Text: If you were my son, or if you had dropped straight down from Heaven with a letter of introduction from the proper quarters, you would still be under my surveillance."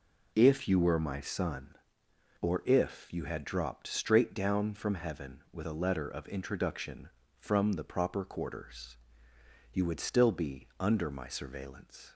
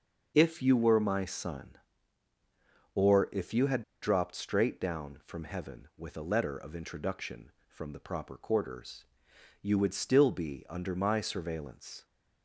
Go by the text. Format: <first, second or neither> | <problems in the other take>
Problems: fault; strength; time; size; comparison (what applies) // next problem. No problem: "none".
first | starts louder than the rest; until 1.3 s; 6.5 dB // pauses between "had" and "dropped"; slight; at 3.8 s; 0.21 s long